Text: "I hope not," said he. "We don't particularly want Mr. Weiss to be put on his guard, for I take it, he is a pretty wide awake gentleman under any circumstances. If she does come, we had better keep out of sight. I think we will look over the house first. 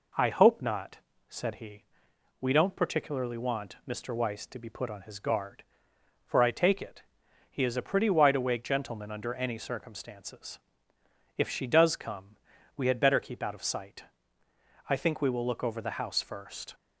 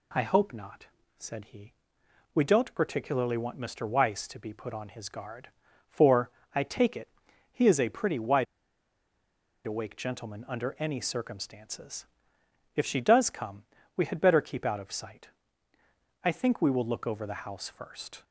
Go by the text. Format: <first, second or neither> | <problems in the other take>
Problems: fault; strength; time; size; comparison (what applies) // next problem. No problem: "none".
first | pauses between "for" and "I"; slight; at 6.2 s; 0.24 s long // pauses between "wide" and "awake"; at 8.4 s; 1.2 s long